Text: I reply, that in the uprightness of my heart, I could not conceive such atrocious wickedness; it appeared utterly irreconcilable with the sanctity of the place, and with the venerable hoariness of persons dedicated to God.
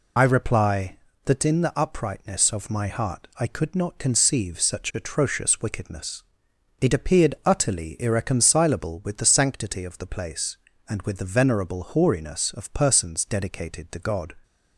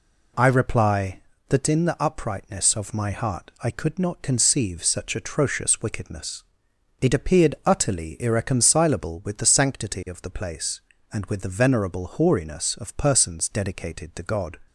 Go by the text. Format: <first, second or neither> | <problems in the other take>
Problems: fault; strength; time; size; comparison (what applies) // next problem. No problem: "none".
second | loses the start of "I"; at 0.1 s; 50 ms